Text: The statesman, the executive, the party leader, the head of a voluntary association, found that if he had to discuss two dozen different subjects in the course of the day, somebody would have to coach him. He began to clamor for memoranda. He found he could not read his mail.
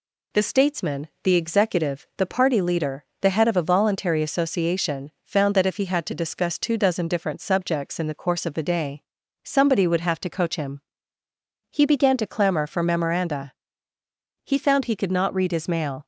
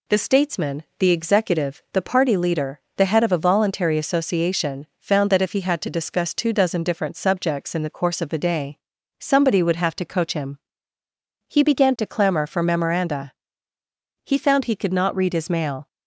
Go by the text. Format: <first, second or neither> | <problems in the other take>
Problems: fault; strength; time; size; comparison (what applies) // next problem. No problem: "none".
neither | none